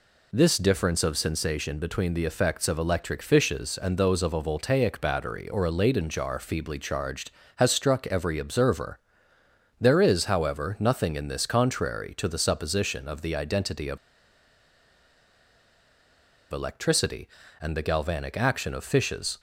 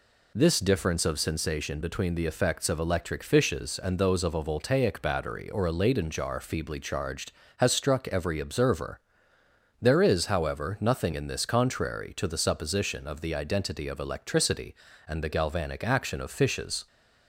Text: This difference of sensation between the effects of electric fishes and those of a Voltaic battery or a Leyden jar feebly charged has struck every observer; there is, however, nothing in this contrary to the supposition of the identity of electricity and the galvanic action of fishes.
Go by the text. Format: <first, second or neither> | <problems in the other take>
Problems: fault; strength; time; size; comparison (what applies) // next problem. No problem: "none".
second | pauses between "of" and "electricity"; strong; at 13.9 s; 2.5 s long